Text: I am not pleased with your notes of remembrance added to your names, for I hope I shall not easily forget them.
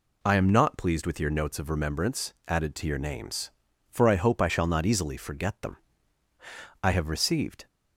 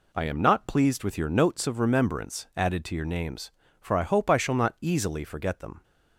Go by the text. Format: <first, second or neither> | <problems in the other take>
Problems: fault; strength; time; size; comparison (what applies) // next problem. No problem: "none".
second | goes on to say "I have received"; noticeable; from 6.8 s on; 0.84 s long